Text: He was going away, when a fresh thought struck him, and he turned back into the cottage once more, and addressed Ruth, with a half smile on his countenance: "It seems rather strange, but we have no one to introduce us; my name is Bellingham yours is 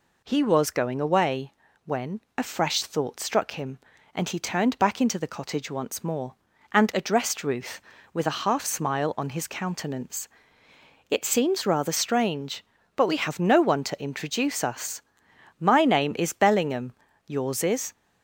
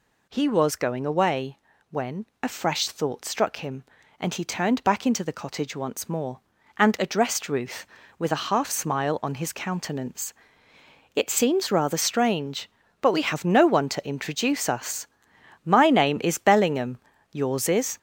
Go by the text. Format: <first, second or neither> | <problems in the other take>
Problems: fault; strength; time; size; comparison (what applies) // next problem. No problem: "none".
first | gets louder; noticeable; throughout; 6 dB // pauses between "when" and "a"; slight; at 2.2 s; 0.16 s long; slight in the first // pauses between "Bellingham" and "yours"; slight; at 16.9 s; 0.34 s long; slight in the first